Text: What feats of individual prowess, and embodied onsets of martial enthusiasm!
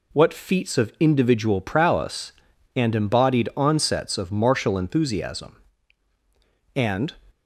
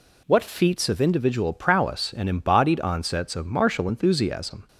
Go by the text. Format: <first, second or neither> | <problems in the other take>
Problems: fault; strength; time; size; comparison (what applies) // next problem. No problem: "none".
second | goes on to say "And"; slight; from 6.7 s on; 0.42 s long